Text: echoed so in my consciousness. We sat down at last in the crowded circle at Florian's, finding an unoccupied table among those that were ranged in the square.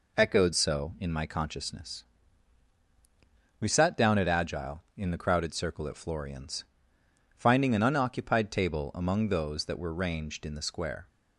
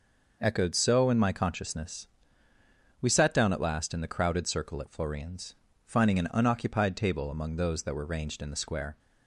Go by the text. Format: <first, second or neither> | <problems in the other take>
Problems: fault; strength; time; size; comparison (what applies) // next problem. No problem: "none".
second | says "agile" for "last"; at 4.2 s